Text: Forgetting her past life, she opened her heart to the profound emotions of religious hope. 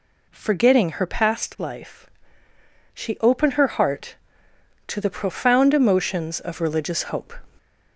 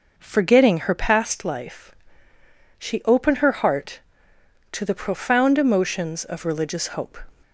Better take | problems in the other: second | gets louder; throughout; 3.5 dB

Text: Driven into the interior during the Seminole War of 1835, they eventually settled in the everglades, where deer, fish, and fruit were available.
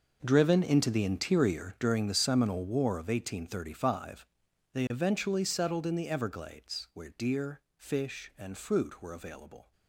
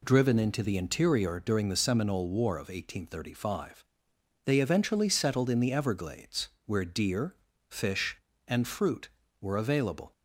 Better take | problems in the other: second | gets quieter; strong; throughout; 14.5 dB

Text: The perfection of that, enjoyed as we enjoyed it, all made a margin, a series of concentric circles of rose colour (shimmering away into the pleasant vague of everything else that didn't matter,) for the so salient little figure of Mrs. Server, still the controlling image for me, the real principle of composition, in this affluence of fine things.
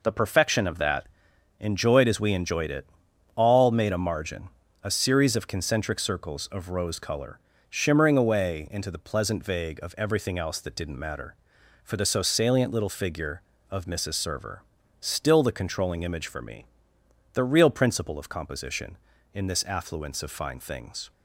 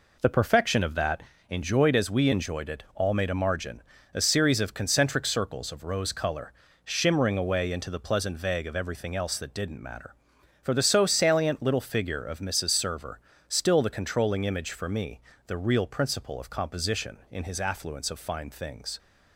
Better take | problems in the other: first | says "his" for "this"; at 17.4 s

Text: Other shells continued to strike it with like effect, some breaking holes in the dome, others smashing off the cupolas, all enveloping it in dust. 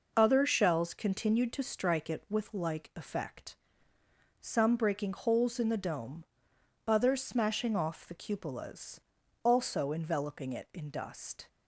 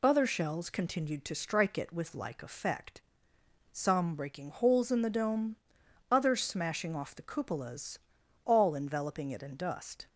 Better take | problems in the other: second | says "also" for "all"; at 9.4 s

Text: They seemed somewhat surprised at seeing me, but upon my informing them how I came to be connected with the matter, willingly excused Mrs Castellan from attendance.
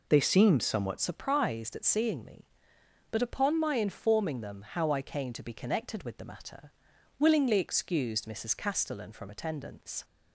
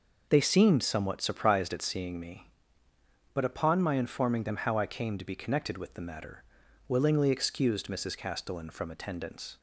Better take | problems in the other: second | changes voice at "surprised"; from 1.0 s on; 9.0 s long

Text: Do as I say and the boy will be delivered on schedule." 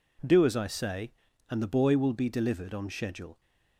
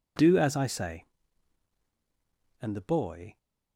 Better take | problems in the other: first | stops before "will be delivered on schedule"; at 3.3 s

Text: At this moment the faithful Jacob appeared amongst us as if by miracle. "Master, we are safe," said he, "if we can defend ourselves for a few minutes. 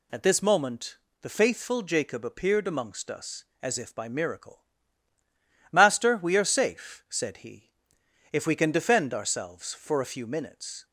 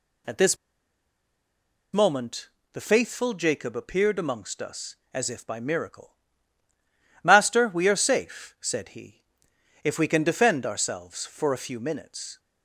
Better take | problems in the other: first | pauses between "this" and "moment"; strong; at 0.5 s; 1.3 s long // pauses between "moment" and "the"; slight; at 2.4 s; 0.24 s long; slight in the first

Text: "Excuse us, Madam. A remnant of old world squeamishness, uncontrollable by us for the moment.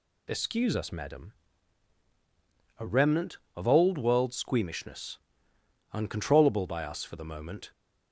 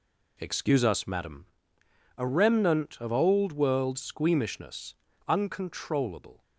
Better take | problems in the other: first | stops before "by us for the moment"; at 6.4 s

